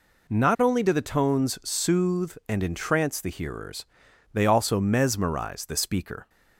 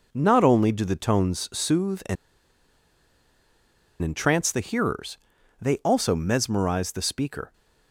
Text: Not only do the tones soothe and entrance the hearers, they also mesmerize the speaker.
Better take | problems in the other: first | pauses between "and" and "entrance"; strong; at 2.1 s; 1.8 s long

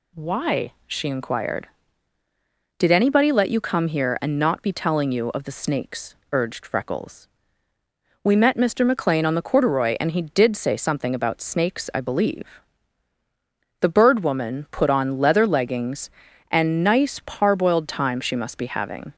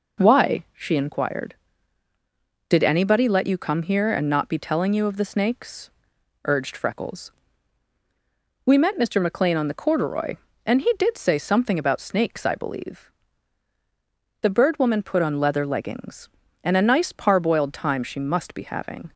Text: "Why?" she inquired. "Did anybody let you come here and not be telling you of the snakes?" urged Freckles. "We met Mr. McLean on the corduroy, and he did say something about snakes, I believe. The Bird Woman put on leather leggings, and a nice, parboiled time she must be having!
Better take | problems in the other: second | skips "a"; at 16.8 s

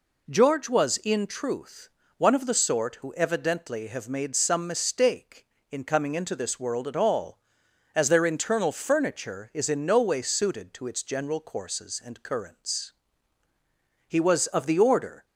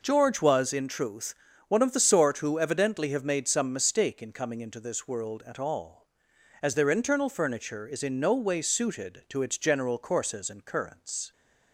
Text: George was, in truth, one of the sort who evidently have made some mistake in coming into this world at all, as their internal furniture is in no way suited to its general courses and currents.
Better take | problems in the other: second | goes on to say "He was of the order"; noticeable; from 14.0 s on; 1.1 s long

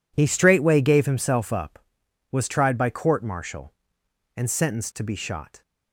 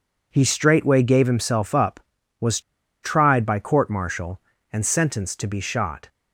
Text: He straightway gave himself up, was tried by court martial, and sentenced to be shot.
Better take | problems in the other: first | pauses between "was" and "tried"; at 2.5 s; 0.43 s long

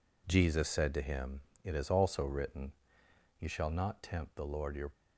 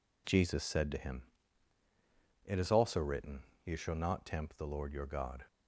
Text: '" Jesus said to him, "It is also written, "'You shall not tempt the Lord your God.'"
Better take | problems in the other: second | stops before "God"; at 4.9 s

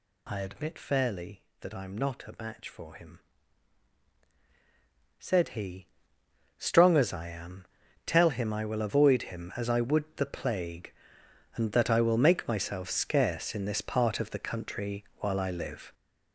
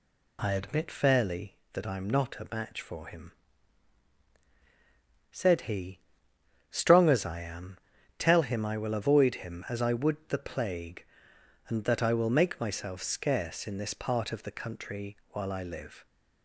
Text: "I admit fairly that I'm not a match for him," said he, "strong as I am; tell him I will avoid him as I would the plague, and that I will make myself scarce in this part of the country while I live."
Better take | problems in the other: second | gets louder; strong; throughout; 7.5 dB

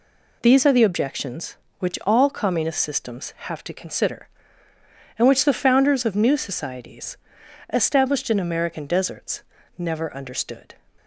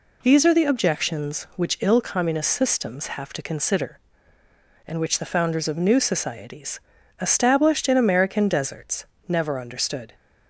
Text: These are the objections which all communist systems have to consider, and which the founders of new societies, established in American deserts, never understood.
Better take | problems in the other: first | says "ill" for "all"; at 1.8 s

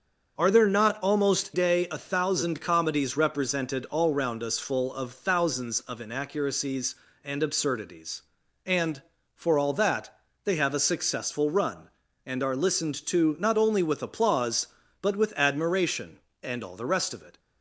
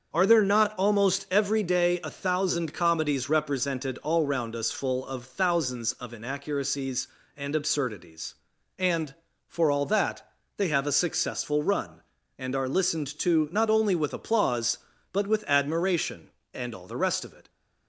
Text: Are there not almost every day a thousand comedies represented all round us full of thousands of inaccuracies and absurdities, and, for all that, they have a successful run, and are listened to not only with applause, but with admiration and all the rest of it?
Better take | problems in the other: second | starts louder than the rest; until 1.3 s; 6.5 dB; also in the second // skips "every"; at 1.5 s

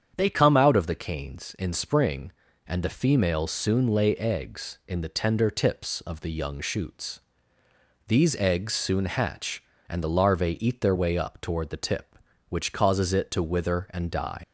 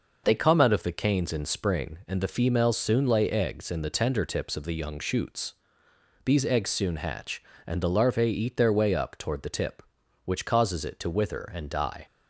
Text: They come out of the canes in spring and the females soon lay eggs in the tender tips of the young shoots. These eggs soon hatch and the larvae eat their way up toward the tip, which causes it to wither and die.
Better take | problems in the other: second | starts louder than the rest; strong; until 1.1 s; 8 dB // leaves "die" unfinished; at 14.4 s; 75 ms

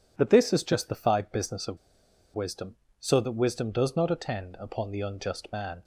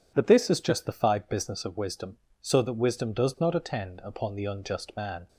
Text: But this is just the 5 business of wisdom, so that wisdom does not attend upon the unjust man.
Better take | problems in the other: second | pauses between "of" and "wisdom"; noticeable; at 1.7 s; 0.55 s long

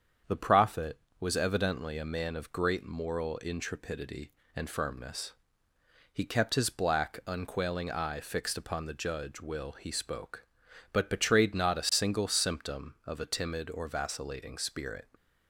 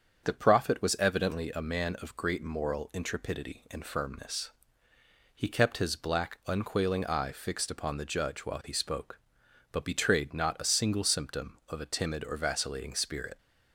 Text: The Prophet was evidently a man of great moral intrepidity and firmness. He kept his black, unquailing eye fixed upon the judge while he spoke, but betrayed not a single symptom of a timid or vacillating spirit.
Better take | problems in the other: second | starts louder than the rest; strong; until 1.4 s; 7.5 dB; strong in the second // says "will" for "while"; at 9.4 s

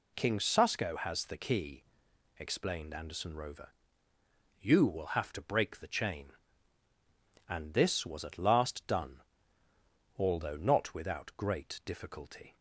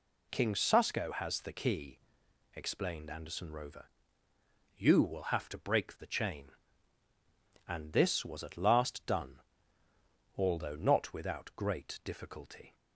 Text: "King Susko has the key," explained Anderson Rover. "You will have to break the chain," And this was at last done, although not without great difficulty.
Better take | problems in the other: neither | none

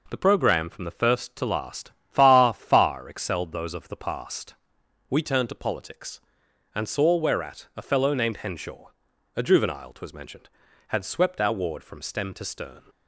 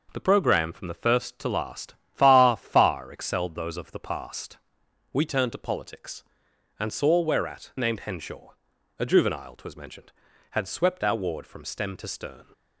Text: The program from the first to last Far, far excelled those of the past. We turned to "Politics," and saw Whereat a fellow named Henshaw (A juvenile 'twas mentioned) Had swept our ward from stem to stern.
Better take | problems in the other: first | pauses between "last" and "Far"; slight; at 1.9 s; 0.18 s long; slight in the first // skips "a fellow"; at 7.7 s

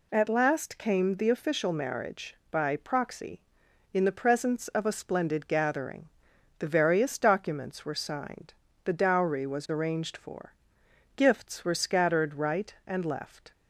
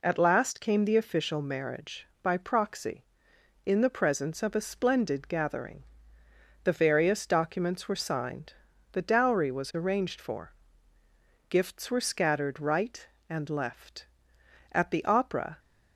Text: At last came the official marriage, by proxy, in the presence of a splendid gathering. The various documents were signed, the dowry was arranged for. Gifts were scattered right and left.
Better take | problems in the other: first | goes on to say "At the opera"; noticeable; from 14.7 s on; 0.88 s long

